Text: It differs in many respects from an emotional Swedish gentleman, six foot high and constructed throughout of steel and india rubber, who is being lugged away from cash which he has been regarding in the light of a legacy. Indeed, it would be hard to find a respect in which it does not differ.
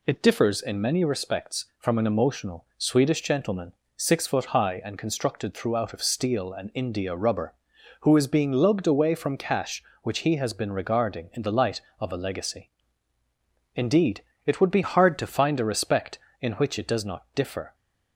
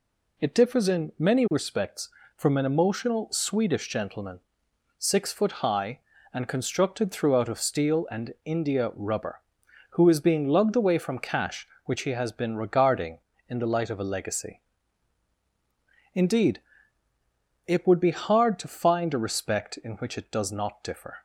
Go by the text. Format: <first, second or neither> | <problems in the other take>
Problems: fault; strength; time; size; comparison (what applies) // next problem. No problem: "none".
second | changes voice from "hard" to "to"; from 14.8 to 15.2 s; 0.4 s long